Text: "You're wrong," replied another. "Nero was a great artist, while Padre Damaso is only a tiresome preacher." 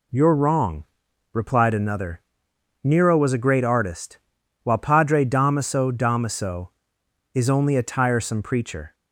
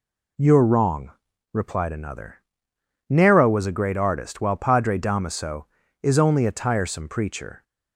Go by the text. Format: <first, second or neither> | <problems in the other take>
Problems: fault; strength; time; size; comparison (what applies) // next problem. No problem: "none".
second | says "Damaso" twice; at 5.9 s